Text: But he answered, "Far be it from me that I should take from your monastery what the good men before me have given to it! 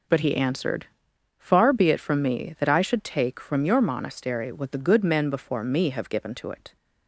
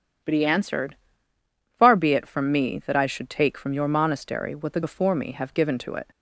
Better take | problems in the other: first | skips "good men"; at 4.8 s

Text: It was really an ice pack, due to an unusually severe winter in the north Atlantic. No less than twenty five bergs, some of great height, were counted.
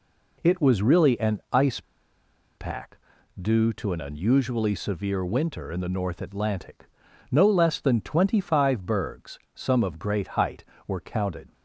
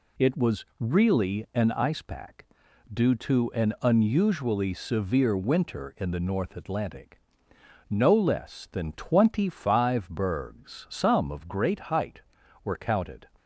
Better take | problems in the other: second | pauses between "ice" and "pack"; noticeable; at 1.8 s; 0.76 s long

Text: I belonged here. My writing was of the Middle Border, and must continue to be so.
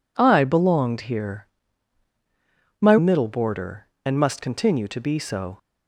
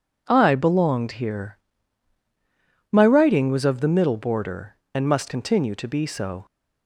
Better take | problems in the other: second | skips "writing was of the"; at 2.9 s

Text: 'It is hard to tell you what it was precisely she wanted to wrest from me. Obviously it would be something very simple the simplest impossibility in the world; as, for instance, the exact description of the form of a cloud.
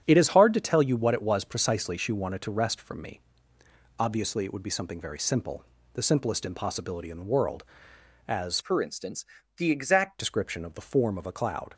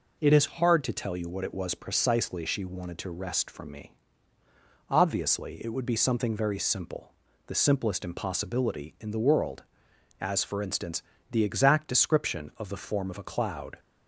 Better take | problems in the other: second | starts louder than the rest; strong; until 1.0 s; 8 dB // pauses between "simple" and "the"; slight; at 5.6 s; 0.30 s long; slight in the second // changes voice from "for" to "exact"; from 8.6 to 10.1 s; 1.5 s long

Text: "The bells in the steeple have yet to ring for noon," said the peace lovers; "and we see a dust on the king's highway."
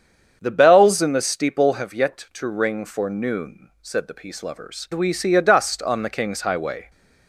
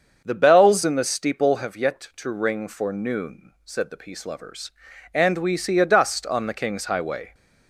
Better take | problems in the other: second | starts louder than the rest; strong; until 1.4 s; 7.5 dB; also in the second // skips "and"; at 4.8 s

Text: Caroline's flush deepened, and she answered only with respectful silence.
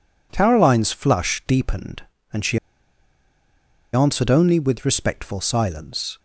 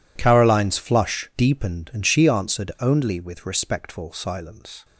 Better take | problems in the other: second | pauses between "she" and "answered"; strong; at 2.5 s; 1.3 s long

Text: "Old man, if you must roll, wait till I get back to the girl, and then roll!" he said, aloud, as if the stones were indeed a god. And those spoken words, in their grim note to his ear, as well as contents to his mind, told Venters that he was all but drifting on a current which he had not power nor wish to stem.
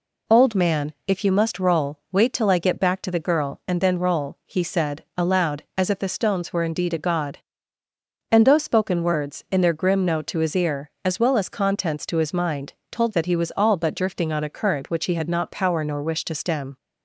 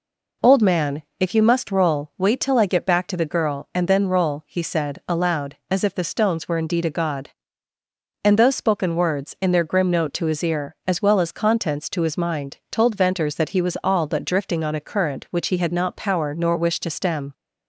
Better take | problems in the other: second | skips "Venters"; at 13.1 s

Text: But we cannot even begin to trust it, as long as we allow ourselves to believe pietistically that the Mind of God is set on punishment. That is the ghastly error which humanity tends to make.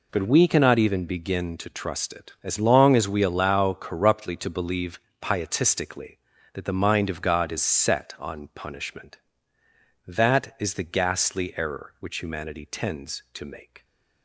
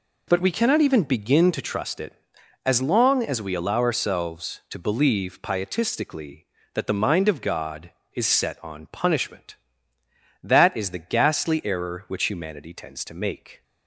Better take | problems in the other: second | says "corruptly" for "ourselves"; at 3.7 s // pauses between "believe" and "pietistically"; slight; at 4.9 s; 0.24 s long

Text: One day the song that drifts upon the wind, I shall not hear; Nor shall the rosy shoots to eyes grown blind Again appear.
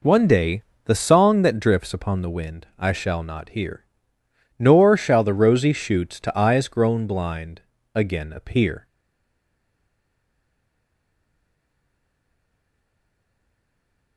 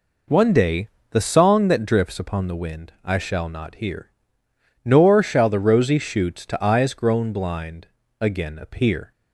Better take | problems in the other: second | pauses between "day" and "the"; slight; at 0.6 s; 0.20 s long; slight in the second // pauses between "blind" and "Again"; slight; at 7.6 s; 0.34 s long; slight in the second // stays silent after the last word; strong; from 8.8 s on; 5.3 s long

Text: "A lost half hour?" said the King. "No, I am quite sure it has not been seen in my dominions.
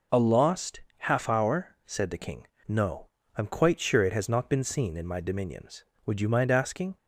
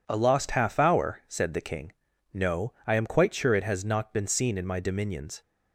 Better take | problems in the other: second | pauses between "lost" and "half"; slight; at 0.8 s; 0.18 s long // goes on to say "Would you mind asking"; noticeable; from 6.0 s on; 0.90 s long

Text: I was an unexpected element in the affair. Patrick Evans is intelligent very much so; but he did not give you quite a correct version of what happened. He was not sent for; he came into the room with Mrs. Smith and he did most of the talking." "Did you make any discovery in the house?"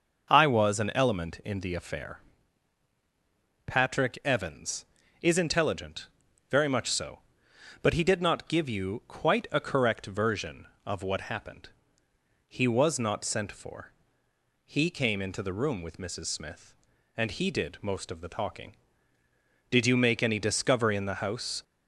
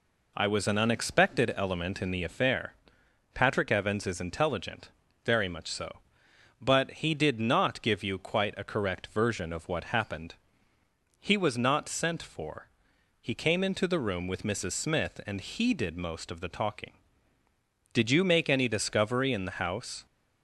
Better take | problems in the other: second | skips "unexpected"; at 0.9 s // pauses between "intelligent" and "very"; at 6.0 s; 0.44 s long; slight in the second

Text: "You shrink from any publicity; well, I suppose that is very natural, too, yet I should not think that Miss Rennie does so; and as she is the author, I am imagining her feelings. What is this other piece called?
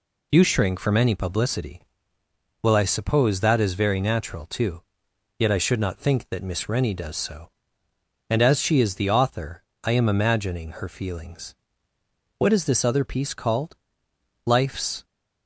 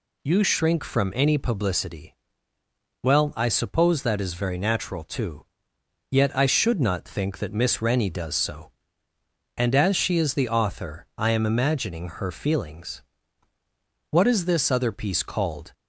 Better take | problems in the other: second | goes on to say "Life's"; from 14.4 s on; 0.58 s long

